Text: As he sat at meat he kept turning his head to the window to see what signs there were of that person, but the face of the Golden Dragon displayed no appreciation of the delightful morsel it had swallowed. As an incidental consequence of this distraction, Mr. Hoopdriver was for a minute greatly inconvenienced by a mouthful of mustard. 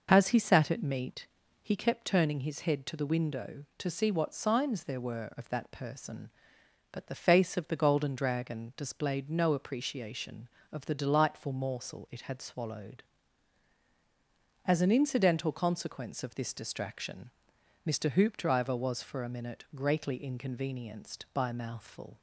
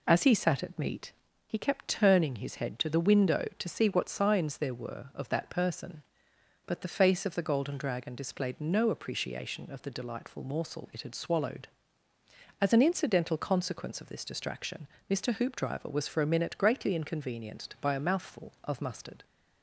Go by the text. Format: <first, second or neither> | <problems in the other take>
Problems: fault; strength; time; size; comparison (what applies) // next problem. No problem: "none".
second | pauses between "meat" and "he"; slight; at 1.2 s; 0.34 s long; slight in the second // stops before "of mustard"; at 22.1 s